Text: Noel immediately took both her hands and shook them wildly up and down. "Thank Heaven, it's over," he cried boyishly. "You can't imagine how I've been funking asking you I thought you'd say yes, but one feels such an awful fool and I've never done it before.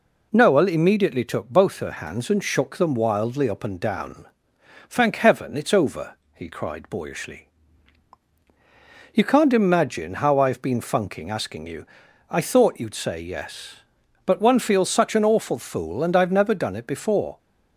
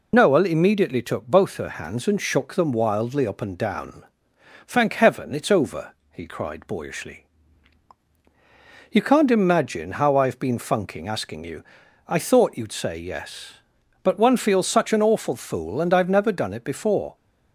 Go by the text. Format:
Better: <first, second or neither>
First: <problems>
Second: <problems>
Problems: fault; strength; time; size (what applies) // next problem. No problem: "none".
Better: first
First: pauses between "you" and "I"; at 11.8 s; 0.44 s long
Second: loses the start of "Noel"; at 0.1 s; 45 ms // pauses between "you" and "I"; at 11.6 s; 0.44 s long